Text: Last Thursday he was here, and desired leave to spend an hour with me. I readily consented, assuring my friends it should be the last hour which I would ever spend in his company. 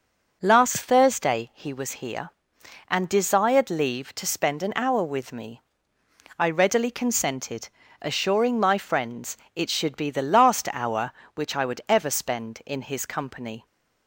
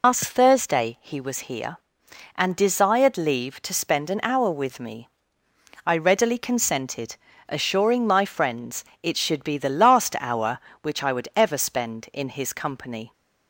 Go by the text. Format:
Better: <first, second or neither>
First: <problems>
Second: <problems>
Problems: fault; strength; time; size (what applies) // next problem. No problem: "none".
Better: first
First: pauses between "friends" and "it"; slight; at 9.3 s; 0.22 s long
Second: loses the start of "Last"; at 0.0 s; 160 ms // pauses between "friends" and "it"; slight; at 8.8 s; 0.22 s long